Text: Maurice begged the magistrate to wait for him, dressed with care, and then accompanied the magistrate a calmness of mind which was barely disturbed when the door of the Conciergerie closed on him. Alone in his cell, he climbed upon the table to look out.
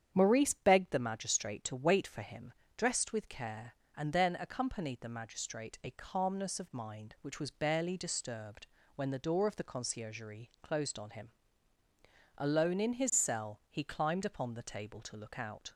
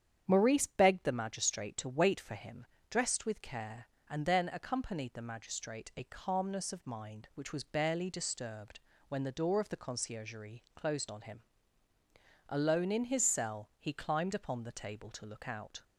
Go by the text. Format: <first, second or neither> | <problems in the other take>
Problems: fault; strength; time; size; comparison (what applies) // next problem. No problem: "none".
neither | starts louder than the rest; strong; the same in both // pauses between "disturbed" and "when"; slight; the same in both